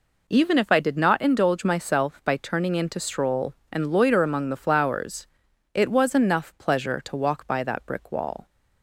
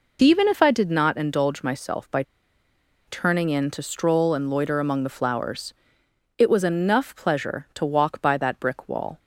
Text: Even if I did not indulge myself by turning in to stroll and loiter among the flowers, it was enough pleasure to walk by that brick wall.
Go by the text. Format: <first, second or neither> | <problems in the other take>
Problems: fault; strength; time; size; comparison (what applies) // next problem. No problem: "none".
first | pauses between "by" and "turning"; noticeable; at 2.2 s; 0.82 s long